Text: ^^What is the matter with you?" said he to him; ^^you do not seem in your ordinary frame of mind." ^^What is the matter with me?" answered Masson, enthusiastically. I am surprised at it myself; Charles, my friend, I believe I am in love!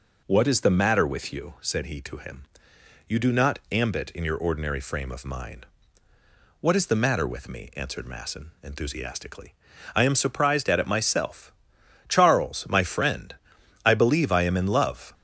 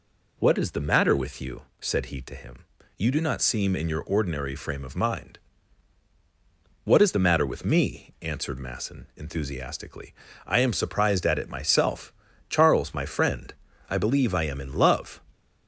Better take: second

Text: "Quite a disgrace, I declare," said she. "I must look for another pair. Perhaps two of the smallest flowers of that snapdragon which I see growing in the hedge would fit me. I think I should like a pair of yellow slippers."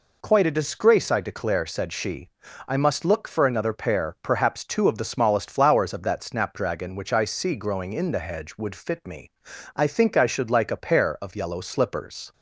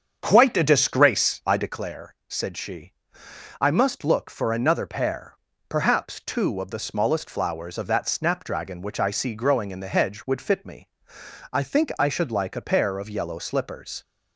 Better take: first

